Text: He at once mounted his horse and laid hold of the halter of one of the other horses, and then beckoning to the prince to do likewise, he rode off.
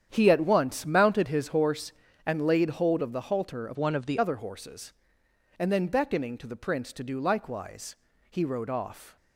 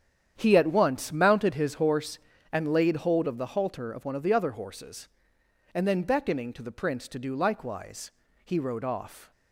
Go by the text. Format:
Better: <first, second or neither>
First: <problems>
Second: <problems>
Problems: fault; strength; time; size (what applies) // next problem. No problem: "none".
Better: second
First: starts louder than the rest; strong; until 1.1 s; 9 dB // changes voice from "one" to "the"; from 3.7 to 4.1 s; 0.4 s long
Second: starts louder than the rest; strong; until 1.3 s; 9 dB